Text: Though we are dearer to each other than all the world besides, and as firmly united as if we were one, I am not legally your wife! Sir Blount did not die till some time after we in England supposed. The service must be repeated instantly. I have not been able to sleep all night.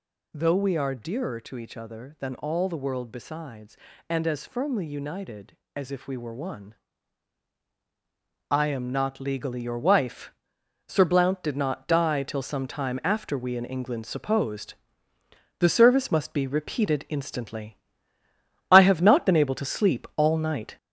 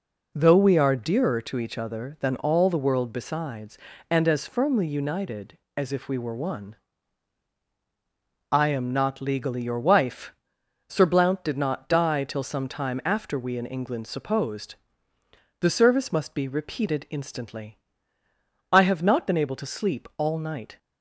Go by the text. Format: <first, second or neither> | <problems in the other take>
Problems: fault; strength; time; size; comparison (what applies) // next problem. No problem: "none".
second | gets louder; noticeable; throughout; 5.5 dB